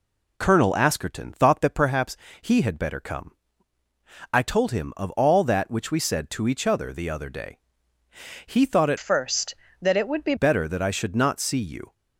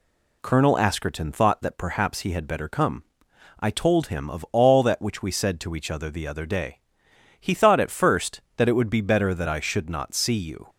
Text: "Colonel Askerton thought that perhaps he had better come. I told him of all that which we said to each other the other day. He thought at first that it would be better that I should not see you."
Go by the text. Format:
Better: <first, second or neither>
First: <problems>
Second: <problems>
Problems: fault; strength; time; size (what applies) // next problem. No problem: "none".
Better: second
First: pauses between "perhaps" and "he"; slight; at 2.1 s; 0.24 s long // changes voice from "first" to "be"; from 8.9 to 10.3 s; 1.4 s long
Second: none